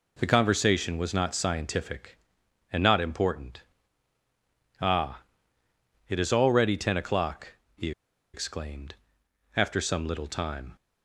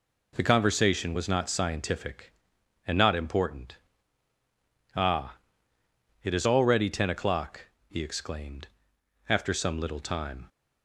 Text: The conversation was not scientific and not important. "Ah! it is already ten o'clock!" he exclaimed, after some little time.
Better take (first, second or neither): second